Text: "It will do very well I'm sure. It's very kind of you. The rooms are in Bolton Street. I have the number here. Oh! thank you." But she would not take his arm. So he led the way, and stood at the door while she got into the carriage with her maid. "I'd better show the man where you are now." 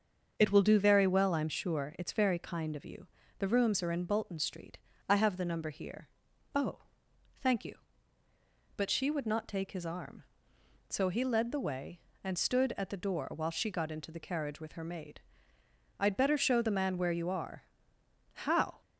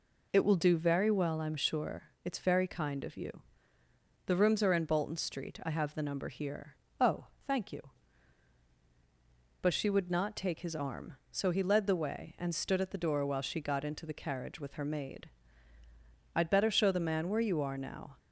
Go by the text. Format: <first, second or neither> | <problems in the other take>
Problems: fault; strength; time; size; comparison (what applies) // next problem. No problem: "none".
second | starts louder than the rest; until 1.3 s; 6.5 dB // says "how" for "now"; at 18.3 s